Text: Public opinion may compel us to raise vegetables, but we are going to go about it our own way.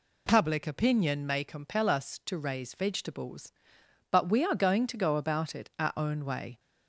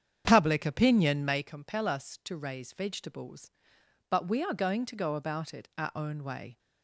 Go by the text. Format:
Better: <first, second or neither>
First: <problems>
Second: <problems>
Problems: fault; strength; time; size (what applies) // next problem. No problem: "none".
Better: first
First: none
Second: starts louder than the rest; strong; until 1.6 s; 8 dB